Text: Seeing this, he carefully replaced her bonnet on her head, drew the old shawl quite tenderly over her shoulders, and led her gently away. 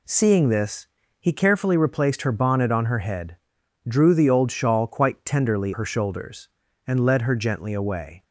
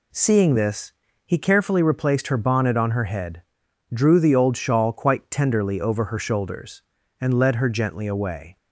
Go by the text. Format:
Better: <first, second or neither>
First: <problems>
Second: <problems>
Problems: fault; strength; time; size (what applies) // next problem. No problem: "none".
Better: second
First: skips "over"; at 5.7 s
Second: none